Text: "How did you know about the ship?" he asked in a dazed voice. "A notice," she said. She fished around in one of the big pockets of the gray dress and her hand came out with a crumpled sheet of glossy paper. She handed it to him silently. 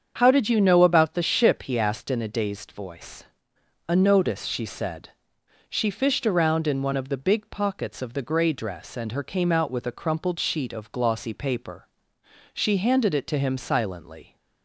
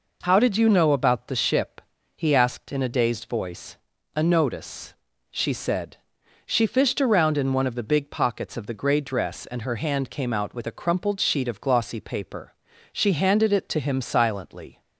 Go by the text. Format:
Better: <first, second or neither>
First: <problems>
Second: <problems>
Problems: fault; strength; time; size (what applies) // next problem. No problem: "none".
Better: second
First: starts louder than the rest; strong; until 1.1 s; 7.5 dB // skips "hand"; at 9.2 s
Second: none